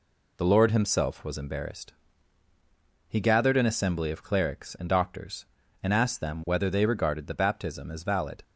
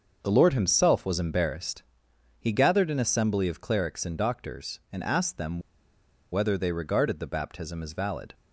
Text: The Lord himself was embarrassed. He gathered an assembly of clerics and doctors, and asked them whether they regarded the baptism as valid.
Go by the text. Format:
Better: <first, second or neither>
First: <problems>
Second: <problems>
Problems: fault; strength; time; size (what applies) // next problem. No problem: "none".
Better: first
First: none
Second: starts louder than the rest; until 1.2 s; 6.5 dB // pauses between "them" and "whether"; noticeable; at 5.6 s; 0.71 s long